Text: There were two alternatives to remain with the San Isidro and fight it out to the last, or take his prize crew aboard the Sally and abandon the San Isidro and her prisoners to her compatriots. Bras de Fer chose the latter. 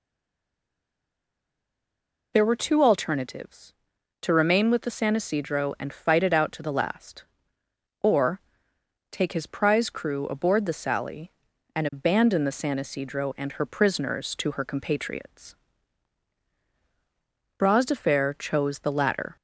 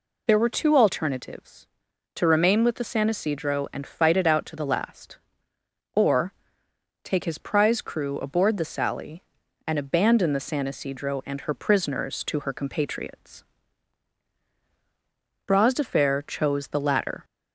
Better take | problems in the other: second | stays silent before the first word; until 2.3 s; 2.3 s long // pauses between "or" and "take"; noticeable; at 8.4 s; 0.70 s long; noticeable in the second

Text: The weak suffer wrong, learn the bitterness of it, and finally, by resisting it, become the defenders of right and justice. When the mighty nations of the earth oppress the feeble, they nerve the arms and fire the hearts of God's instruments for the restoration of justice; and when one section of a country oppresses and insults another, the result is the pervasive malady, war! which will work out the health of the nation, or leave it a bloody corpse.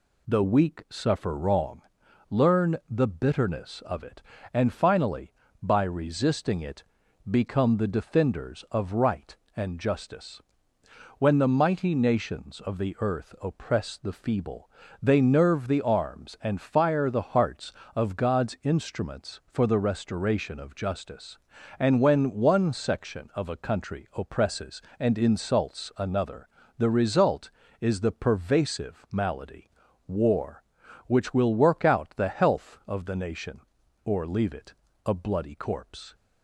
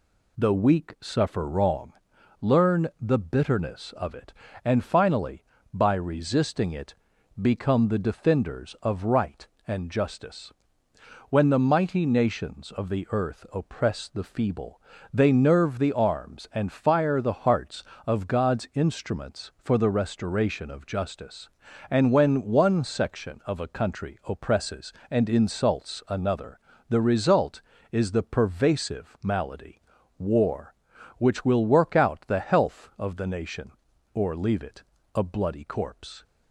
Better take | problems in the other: neither | pauses between "it" and "a"; slight; the same in both

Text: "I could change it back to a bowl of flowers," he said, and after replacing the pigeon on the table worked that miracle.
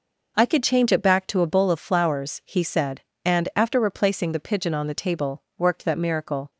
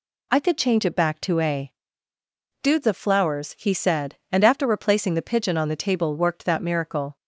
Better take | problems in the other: first | says "dudes" for "bowl"; at 2.6 s

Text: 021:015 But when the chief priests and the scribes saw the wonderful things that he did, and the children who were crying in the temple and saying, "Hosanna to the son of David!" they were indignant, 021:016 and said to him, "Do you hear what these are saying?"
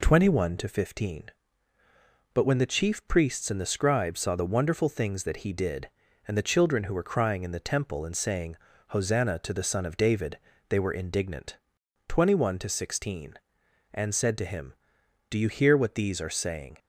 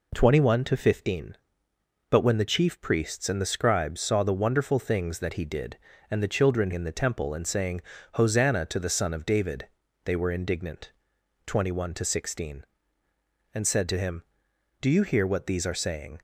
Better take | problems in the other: first | skips "who were crying"; at 6.7 s

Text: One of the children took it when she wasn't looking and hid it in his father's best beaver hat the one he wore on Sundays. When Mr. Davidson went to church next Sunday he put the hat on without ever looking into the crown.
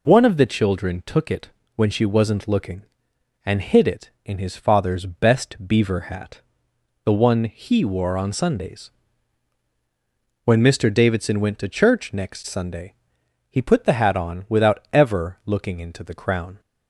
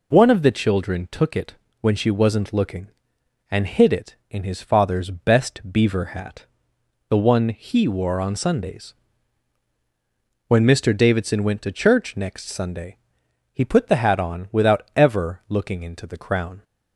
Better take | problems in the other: neither | pauses between "it" and "when"; slight; the same in both // pauses between "hat" and "the"; noticeable; the same in both // pauses between "Sunday" and "he"; noticeable; the same in both

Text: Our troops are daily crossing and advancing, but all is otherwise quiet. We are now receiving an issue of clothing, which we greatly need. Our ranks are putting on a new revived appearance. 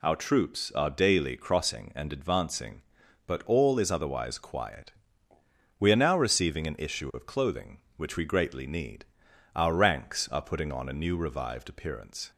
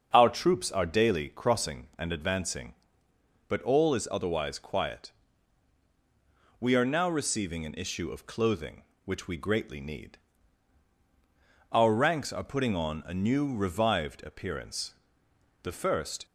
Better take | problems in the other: first | starts louder than the rest; until 1.1 s; 6.5 dB // goes on to say "The first"; noticeable; from 15.6 s on; 0.63 s long

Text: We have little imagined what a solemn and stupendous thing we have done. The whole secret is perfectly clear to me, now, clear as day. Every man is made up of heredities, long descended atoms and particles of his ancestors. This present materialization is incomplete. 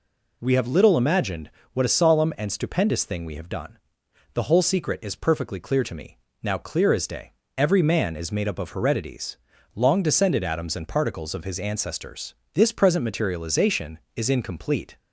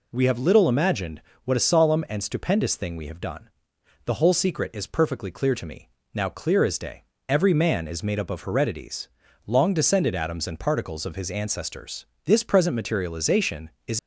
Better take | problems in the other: first | pauses between "imagined" and "what"; slight; at 1.2 s; 0.22 s long; slight in the first // stops before "incomplete"; at 13.9 s

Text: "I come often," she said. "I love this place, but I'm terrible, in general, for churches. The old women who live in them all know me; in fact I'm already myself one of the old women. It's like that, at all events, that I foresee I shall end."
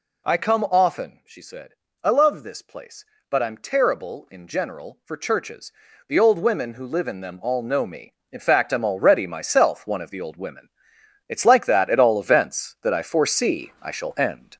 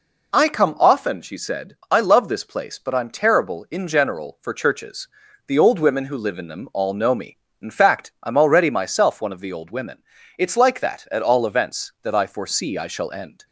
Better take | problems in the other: second | gets louder; noticeable; throughout; 4.5 dB

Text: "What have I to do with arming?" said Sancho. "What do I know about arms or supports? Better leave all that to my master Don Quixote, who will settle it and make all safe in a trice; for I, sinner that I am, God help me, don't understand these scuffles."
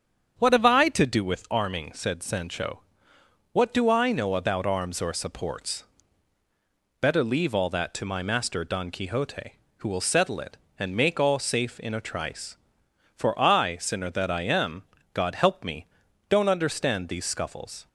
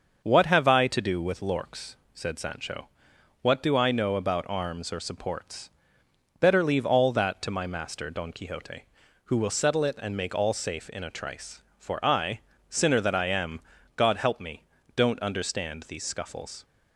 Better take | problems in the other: first | starts louder than the rest; until 1.2 s; 6.5 dB; strong in the first // says "lorks" for "arming"; at 1.3 s

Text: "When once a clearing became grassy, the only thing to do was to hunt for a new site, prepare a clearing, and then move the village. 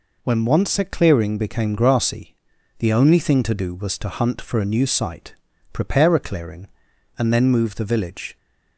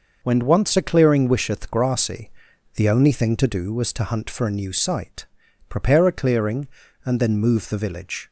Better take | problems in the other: first | says "wisheth" for "became"; at 1.2 s

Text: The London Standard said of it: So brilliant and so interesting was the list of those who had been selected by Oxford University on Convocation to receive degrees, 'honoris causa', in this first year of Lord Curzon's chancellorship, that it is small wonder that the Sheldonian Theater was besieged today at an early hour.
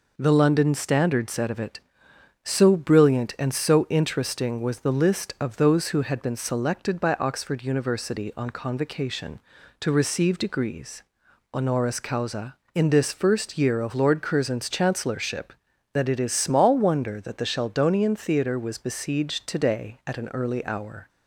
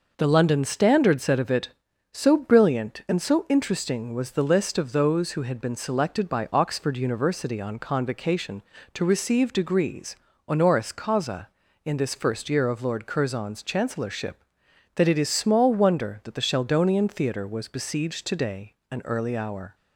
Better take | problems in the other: first | skips "at"; at 18.8 s

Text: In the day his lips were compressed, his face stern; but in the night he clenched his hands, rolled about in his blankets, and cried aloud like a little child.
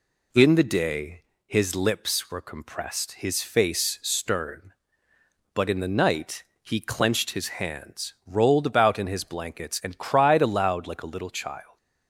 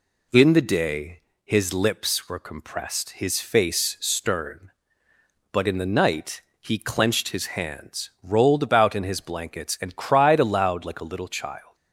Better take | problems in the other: neither | pauses between "day" and "his"; slight; the same in both // pauses between "night" and "he"; slight; the same in both

